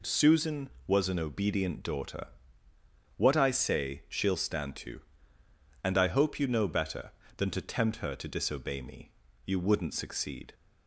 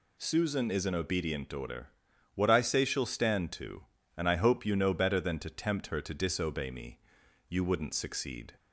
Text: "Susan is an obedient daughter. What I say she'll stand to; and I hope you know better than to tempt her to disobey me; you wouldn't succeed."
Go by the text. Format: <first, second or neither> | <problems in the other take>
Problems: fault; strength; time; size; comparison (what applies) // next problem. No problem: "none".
second | says "was" for "is"; at 0.8 s